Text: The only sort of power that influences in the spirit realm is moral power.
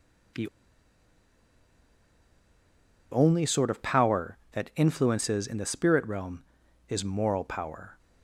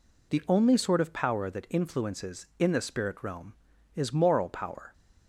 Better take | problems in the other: second | pauses between "The" and "only"; strong; at 0.4 s; 2.6 s long

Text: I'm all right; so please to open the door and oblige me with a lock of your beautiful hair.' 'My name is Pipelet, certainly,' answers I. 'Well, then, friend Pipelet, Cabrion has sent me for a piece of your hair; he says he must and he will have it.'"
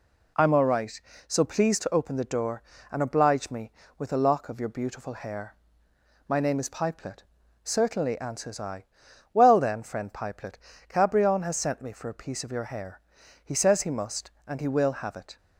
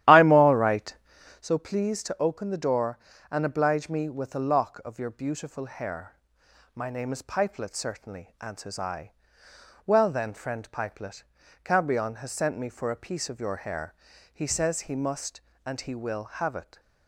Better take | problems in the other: first | starts louder than the rest; strong; until 1.5 s; 12.5 dB

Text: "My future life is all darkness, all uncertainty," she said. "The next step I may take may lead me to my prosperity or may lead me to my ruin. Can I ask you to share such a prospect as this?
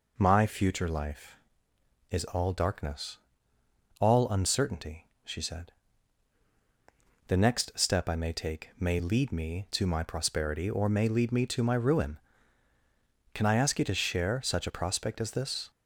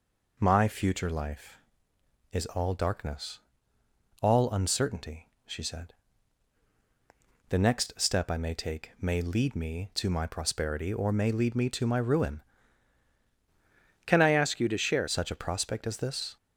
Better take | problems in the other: first | changes voice from "Can" to "share"; from 14.0 to 15.0 s; 1.0 s long

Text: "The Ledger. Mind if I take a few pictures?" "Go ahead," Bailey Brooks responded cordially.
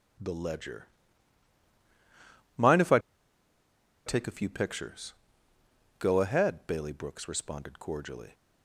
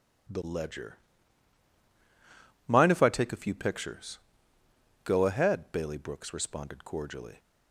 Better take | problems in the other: second | pauses between "I" and "take"; at 2.9 s; 1.0 s long

